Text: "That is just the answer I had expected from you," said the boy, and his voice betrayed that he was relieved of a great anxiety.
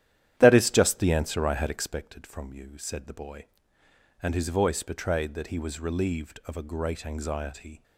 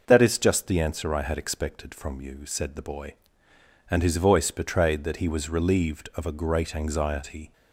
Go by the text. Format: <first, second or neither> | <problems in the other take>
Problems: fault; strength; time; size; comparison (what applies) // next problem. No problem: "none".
second | starts louder than the rest; strong; until 2.0 s; 11.5 dB